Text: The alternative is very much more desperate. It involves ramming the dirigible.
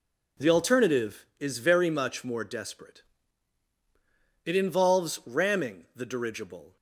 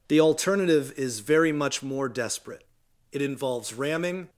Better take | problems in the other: first | stops before "the dirigible"; at 4.2 s

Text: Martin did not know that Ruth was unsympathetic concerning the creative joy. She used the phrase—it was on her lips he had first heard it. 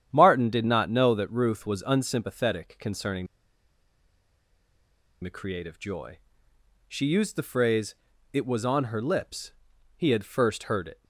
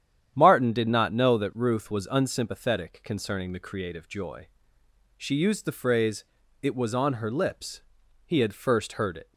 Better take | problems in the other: second | starts louder than the rest; strong; until 1.1 s; 9.5 dB; strong in the second // pauses between "concerning" and "the"; strong; at 3.2 s; 1.9 s long // pauses between "lips" and "he"; at 9.5 s; 0.42 s long; also in the second

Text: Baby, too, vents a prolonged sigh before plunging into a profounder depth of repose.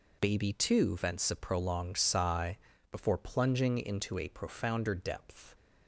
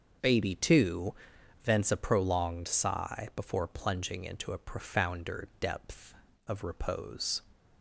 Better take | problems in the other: second | pauses between "sigh" and "before"; slight; at 2.5 s; 0.34 s long // stops before "of repose"; at 5.5 s

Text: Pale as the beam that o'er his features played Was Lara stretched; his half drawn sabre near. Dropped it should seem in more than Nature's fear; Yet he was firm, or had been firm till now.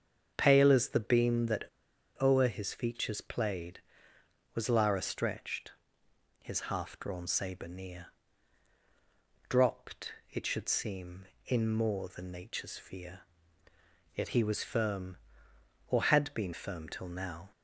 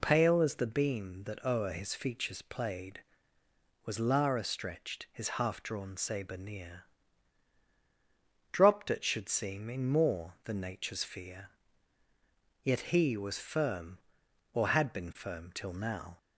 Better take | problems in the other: second | starts louder than the rest; until 1.3 s; 7 dB // pauses between "that" and "o'er"; noticeable; at 1.6 s; 0.56 s long // pauses between "Dropped" and "it"; slight; at 10.1 s; 0.18 s long

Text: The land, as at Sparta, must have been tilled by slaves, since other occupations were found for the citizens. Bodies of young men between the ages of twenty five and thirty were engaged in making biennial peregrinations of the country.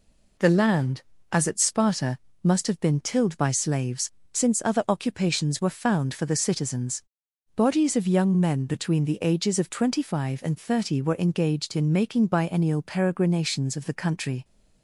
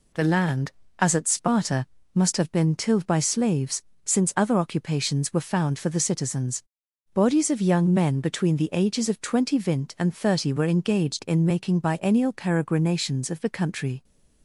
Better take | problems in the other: first | says "vint" for "five"; at 9.5 s

